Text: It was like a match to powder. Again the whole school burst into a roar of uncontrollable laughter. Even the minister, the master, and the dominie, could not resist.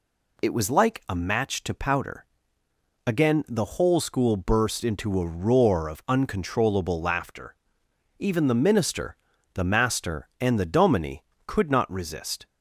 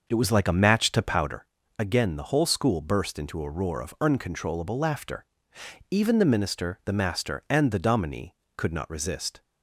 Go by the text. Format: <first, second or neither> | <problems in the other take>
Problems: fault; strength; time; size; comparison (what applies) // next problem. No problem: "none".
first | starts louder than the rest; noticeable; until 1.4 s; 6 dB